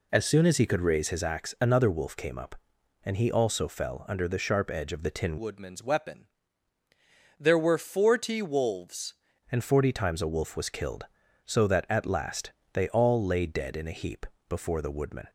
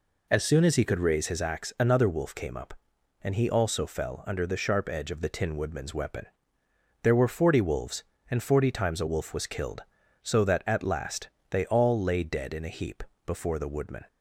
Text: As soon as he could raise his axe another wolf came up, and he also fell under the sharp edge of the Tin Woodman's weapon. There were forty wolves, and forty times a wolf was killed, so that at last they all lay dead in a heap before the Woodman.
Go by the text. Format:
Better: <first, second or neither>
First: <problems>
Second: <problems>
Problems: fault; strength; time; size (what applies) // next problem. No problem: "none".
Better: second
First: changes voice from "Woodman's" to "wolves"; from 5.3 to 9.1 s; 3.8 s long // pauses between "last" and "they"; slight; at 12.5 s; 0.22 s long // pauses between "heap" and "before"; slight; at 14.2 s; 0.24 s long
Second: pauses between "last" and "they"; slight; at 11.2 s; 0.22 s long // pauses between "heap" and "before"; slight; at 13.0 s; 0.24 s long